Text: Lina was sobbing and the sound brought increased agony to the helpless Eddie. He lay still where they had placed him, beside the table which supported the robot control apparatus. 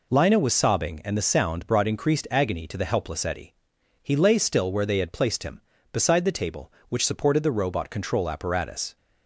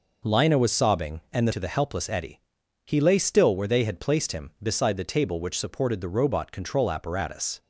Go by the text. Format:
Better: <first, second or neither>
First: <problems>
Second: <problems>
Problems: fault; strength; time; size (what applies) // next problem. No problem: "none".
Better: first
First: none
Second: skips "sound brought increased agony"; at 1.5 s